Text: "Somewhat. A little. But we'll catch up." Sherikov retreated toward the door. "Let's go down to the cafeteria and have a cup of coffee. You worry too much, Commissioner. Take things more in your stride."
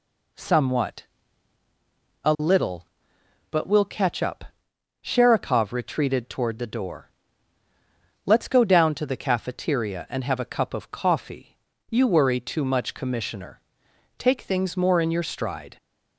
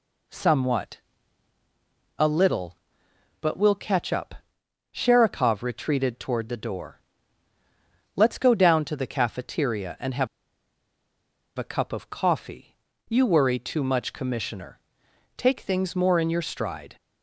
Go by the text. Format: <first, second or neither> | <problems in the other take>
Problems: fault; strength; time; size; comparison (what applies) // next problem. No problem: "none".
first | pauses between "have" and "a"; strong; at 10.2 s; 1.3 s long